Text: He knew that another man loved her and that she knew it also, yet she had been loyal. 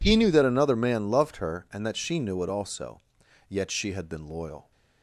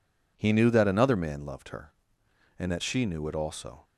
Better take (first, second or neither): first